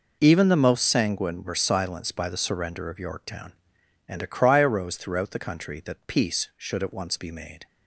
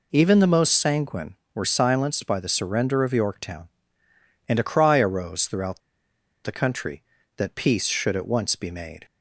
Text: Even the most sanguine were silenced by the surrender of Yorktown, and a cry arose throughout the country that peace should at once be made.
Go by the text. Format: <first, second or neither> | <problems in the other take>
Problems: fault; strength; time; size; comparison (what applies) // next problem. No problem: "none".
first | pauses between "throughout" and "the"; noticeable; at 5.8 s; 0.64 s long